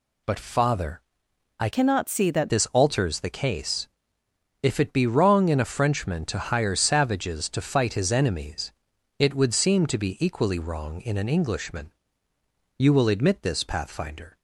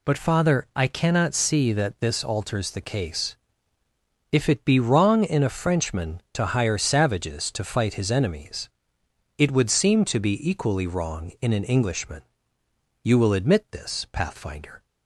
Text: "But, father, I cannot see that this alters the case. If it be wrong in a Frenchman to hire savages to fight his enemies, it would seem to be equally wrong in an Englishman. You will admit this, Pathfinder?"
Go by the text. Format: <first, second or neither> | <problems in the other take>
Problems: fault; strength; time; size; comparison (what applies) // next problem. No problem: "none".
second | changes voice from "cannot" to "that"; from 1.7 to 2.4 s; 0.7 s long